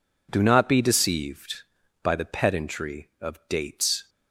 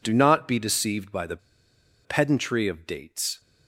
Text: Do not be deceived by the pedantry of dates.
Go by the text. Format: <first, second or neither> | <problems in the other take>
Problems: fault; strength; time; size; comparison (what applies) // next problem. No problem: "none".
first | pauses between "the" and "pedantry"; noticeable; at 1.3 s; 0.67 s long